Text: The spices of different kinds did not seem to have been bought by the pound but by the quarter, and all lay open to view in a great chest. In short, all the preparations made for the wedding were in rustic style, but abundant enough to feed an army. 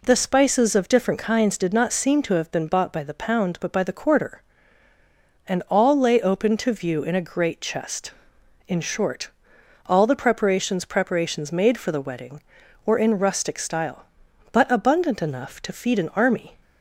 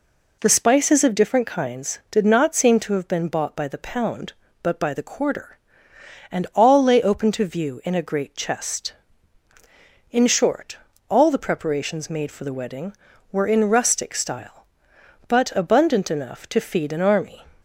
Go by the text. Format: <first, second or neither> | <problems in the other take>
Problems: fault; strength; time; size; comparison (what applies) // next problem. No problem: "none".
second | says "preparations" twice; at 10.8 s